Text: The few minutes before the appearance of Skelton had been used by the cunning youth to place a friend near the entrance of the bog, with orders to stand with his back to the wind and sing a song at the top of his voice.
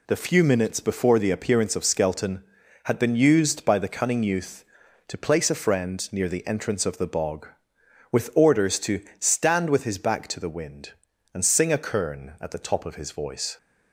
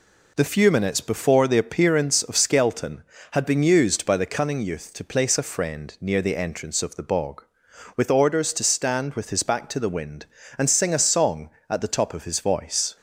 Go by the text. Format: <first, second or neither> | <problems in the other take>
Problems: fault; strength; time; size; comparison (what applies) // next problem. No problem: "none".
second | pauses between "to" and "stand"; slight; at 9.0 s; 0.16 s long // says "kern" for "song"; at 11.7 s